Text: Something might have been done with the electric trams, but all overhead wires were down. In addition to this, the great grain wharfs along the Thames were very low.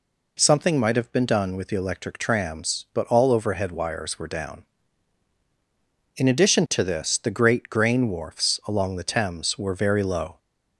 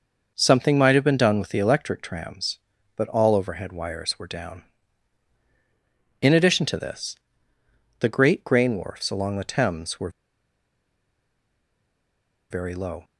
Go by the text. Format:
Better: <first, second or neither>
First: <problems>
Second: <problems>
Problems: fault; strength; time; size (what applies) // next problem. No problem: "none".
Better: first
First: none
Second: pauses between "were" and "very"; strong; at 10.0 s; 2.4 s long